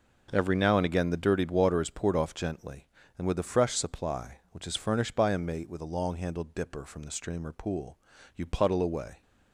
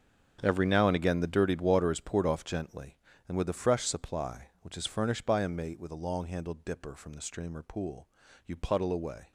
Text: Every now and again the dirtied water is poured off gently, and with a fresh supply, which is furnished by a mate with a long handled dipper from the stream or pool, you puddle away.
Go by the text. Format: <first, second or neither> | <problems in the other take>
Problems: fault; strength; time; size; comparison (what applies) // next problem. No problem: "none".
first | gets quieter; strong; throughout; 15 dB